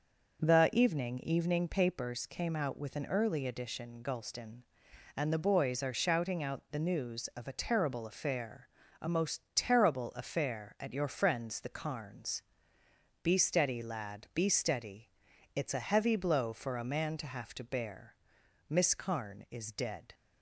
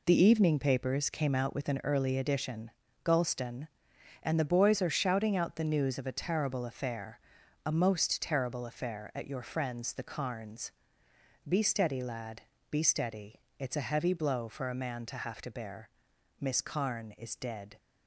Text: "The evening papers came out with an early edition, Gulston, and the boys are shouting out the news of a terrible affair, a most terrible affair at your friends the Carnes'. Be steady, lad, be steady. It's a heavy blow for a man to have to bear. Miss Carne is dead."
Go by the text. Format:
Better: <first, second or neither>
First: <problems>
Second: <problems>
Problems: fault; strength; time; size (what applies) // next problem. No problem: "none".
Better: second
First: says "evening" twice; at 1.1 s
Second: none